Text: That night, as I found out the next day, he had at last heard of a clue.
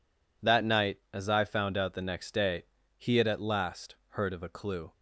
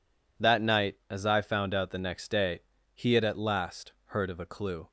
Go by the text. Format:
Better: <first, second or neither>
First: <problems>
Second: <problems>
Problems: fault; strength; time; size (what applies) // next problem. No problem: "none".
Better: neither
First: none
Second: none